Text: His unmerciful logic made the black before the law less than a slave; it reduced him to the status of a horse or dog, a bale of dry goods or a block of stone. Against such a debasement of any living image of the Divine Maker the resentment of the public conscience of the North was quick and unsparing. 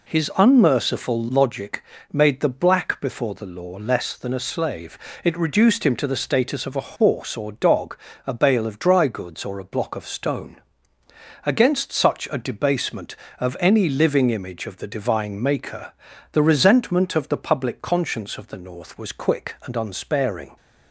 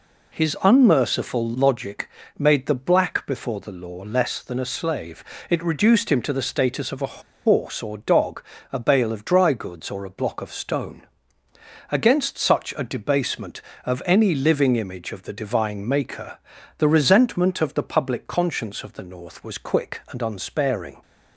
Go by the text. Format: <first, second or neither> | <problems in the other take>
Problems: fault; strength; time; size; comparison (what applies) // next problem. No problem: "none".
first | pauses between "logic" and "made"; slight; at 2.0 s; 0.30 s long; slight in the first // pauses between "a" and "horse"; slight; at 7.1 s; 0.25 s long // pauses between "Maker" and "the"; at 16.3 s; 0.40 s long; also in the first